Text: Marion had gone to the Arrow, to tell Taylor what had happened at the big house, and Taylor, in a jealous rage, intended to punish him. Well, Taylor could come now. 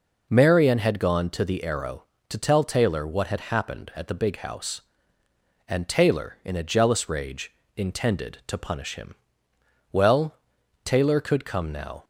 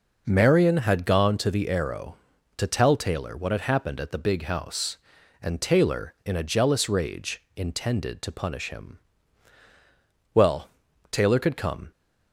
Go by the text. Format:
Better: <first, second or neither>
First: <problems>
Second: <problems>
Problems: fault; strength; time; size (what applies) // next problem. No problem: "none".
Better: first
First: none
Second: stops before "now"; at 11.9 s